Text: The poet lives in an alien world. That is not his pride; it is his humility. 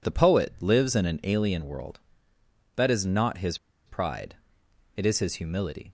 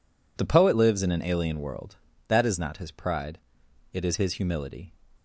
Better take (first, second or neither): second